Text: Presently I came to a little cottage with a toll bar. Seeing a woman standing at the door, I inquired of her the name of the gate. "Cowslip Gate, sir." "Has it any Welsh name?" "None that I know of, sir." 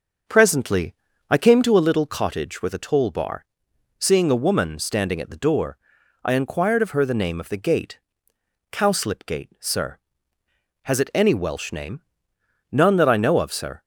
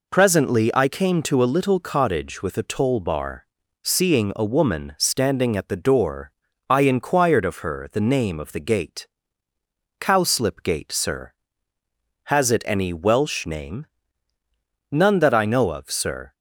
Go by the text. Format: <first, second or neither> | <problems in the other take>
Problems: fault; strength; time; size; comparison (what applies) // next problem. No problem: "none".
second | starts louder than the rest; noticeable; until 1.8 s; 6 dB // pauses between "Presently" and "I"; slight; at 0.9 s; 0.34 s long